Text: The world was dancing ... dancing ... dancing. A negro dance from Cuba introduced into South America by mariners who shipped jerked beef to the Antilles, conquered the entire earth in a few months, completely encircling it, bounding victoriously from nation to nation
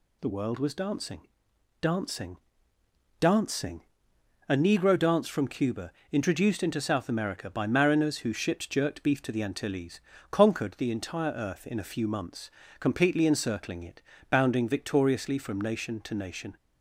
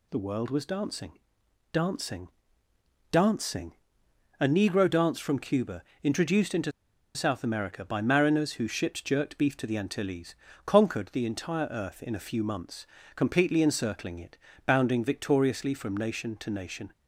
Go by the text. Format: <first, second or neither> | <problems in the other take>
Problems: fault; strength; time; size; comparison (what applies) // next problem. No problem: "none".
first | pauses between "Cuba" and "introduced"; slight; at 5.8 s; 0.20 s long; slight in the first // pauses between "into" and "South"; at 6.7 s; 0.44 s long